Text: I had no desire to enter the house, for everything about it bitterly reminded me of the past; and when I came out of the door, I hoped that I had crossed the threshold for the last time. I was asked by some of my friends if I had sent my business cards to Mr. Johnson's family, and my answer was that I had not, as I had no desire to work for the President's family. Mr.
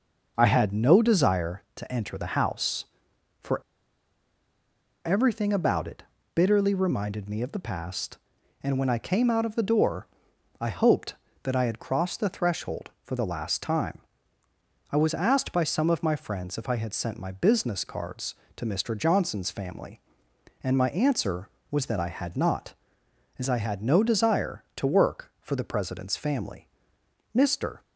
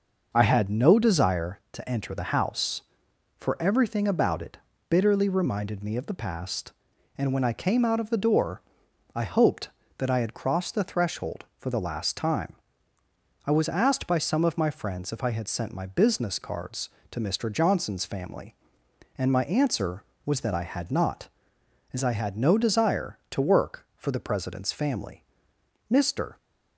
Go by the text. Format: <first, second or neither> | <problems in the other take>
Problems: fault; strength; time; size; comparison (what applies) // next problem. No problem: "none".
second | pauses between "for" and "everything"; strong; at 3.6 s; 1.4 s long // pauses between "it" and "bitterly"; slight; at 6.0 s; 0.30 s long; slight in the second